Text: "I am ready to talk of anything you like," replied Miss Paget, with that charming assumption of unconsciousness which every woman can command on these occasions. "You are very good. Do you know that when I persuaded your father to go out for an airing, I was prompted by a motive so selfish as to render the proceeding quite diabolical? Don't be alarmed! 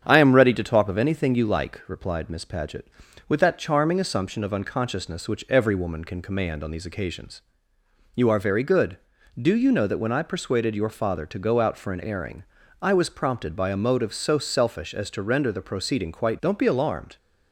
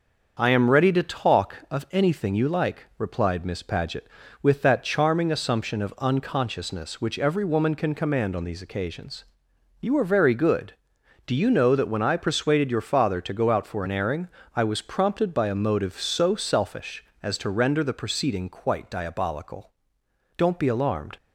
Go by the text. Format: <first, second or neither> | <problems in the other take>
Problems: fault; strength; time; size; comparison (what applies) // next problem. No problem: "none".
second | starts louder than the rest; strong; until 1.0 s; 8.5 dB; also in the second // skips "diabolical"; at 16.3 s